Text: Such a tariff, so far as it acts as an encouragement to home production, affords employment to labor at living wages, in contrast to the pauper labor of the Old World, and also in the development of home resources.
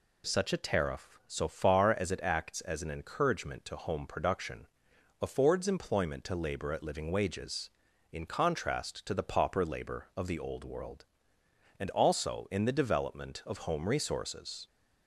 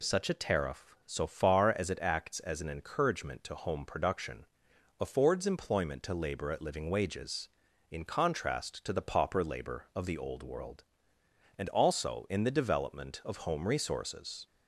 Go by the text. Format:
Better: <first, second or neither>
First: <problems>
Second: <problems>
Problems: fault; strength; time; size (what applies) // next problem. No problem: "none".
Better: neither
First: none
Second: none